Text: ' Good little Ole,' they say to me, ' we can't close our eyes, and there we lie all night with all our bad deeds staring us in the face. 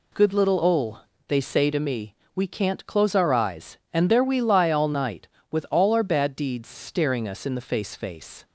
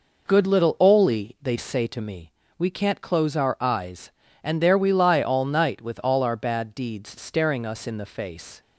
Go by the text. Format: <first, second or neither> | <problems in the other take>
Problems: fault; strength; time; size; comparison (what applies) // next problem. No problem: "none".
second | says "face" twice; at 7.9 s